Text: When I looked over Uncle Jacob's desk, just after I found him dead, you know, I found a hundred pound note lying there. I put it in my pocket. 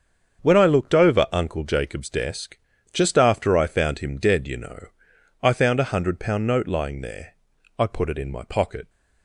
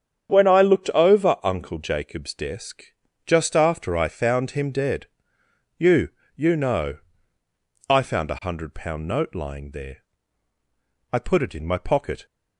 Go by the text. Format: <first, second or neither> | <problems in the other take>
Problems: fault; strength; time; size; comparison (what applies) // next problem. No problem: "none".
first | starts louder than the rest; strong; until 1.4 s; 8 dB; strong in the first // says "you" twice; at 6.3 s